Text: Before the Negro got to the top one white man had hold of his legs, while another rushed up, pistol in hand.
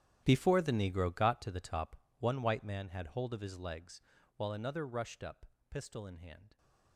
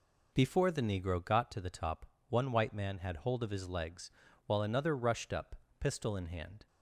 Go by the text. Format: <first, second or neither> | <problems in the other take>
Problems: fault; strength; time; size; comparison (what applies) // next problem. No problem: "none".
second | gets quieter; strong; throughout; 18 dB // pauses between "top" and "one"; slight; at 1.9 s; 0.24 s long; slight in the second